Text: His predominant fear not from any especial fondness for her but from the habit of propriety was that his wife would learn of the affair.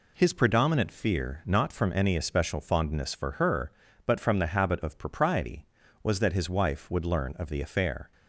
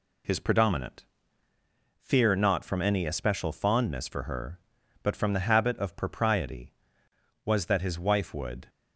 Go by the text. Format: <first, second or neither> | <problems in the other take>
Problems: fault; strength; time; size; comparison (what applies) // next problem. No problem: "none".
first | pauses between "predominant" and "fear"; noticeable; at 1.0 s; 0.94 s long // stops before "learn of the affair"; at 8.6 s